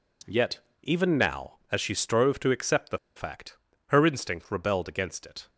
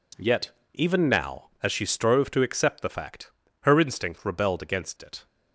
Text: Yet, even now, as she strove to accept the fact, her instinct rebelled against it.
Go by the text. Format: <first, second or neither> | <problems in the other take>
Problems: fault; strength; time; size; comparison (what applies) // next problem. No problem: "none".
second | pauses between "the" and "fact"; slight; at 2.9 s; 0.17 s long